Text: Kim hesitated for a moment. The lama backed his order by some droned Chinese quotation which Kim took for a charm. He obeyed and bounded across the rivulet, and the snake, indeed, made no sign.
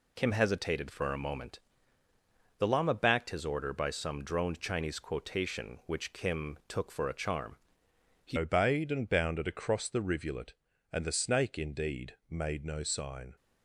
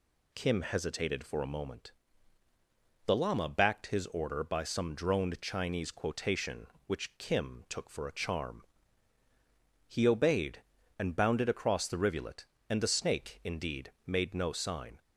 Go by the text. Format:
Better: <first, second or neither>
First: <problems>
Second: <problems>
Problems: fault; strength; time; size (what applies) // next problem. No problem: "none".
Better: second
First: changes voice at "obeyed"; from 8.3 s on; 5.0 s long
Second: none